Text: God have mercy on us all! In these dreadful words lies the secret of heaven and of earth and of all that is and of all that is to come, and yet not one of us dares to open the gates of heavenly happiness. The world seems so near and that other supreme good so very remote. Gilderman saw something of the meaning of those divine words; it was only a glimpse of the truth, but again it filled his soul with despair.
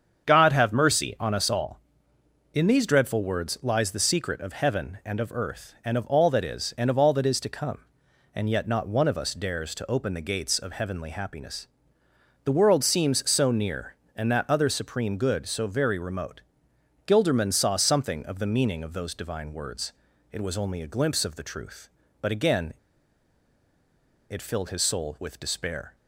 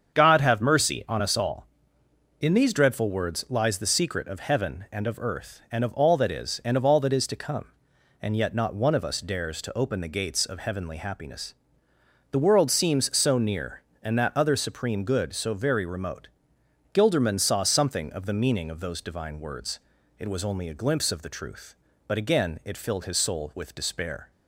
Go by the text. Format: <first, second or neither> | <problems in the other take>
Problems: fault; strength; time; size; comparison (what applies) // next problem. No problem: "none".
second | starts louder than the rest; strong; until 1.2 s; 7 dB; strong in the second // pauses between "again" and "it"; strong; at 22.7 s; 1.5 s long